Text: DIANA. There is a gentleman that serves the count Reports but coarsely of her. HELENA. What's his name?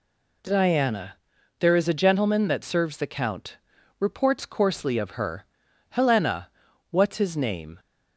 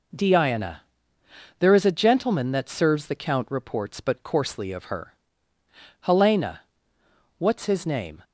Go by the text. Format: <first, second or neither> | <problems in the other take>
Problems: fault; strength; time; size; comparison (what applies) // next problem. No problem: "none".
second | pauses between "count" and "Reports"; at 3.5 s; 0.42 s long // skips "but"; at 4.4 s